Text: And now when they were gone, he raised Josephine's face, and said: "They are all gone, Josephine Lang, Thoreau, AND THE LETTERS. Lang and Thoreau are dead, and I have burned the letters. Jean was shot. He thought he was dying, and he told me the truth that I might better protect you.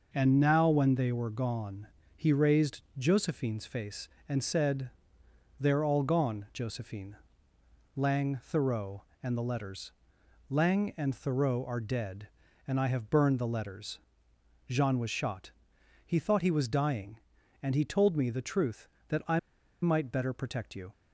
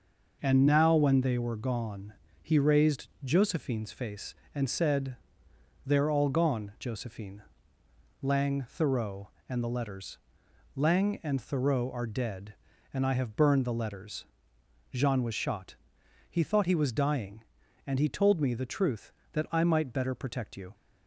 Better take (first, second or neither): second